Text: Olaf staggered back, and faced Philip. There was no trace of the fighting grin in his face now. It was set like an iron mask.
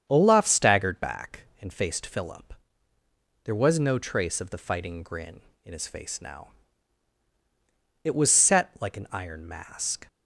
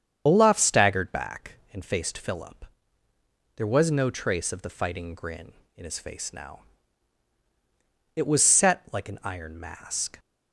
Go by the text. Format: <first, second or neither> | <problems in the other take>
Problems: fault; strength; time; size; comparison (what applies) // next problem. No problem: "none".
first | loses the start of "Olaf"; at 0.2 s; 45 ms // starts louder than the rest; strong; until 1.2 s; 8 dB; strong in the first